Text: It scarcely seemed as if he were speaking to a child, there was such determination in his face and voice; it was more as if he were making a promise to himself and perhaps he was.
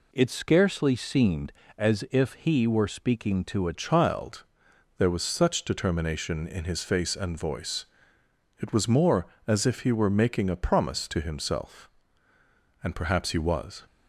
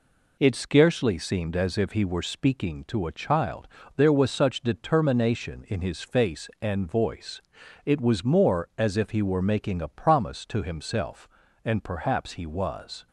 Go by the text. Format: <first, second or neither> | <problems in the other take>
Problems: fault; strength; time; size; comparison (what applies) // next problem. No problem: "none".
second | changes voice at "child"; from 3.7 s on; 10.1 s long